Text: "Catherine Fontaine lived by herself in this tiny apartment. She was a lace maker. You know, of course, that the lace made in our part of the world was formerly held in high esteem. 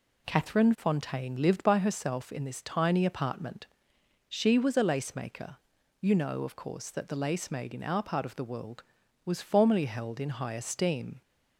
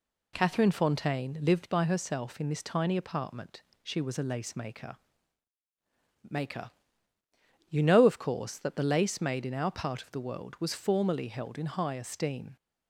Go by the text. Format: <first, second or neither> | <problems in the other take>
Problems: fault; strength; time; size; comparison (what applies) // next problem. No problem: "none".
first | says "maker" twice; at 6.2 s